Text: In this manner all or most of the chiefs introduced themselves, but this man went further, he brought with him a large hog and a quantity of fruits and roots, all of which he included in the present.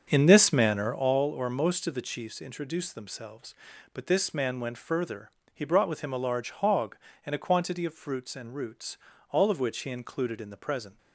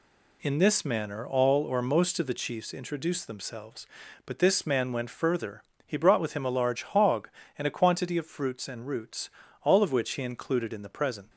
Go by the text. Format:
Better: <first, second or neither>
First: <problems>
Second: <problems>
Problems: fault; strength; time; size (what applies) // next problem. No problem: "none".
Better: second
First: starts louder than the rest; strong; until 1.1 s; 7 dB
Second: none